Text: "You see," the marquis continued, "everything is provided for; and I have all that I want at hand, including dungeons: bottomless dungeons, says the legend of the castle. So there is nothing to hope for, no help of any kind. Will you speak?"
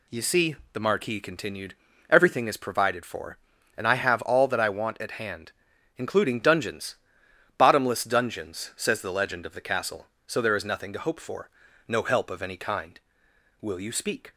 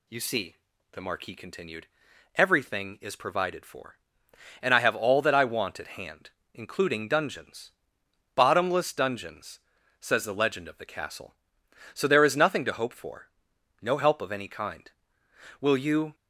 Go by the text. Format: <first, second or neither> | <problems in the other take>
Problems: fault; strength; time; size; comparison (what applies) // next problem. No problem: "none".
first | stops before "speak"; at 16.1 s